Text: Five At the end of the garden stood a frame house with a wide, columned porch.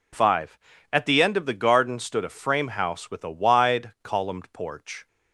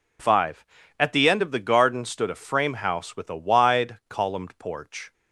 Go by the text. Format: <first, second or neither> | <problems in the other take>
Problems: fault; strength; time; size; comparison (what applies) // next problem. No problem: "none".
neither | none